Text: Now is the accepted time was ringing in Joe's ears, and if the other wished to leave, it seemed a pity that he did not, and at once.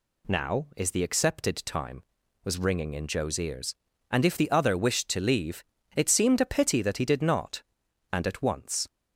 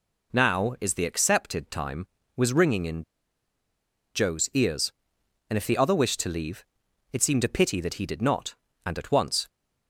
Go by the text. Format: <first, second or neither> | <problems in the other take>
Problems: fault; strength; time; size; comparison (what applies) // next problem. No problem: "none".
first | pauses between "in" and "Joe's"; at 3.0 s; 1.1 s long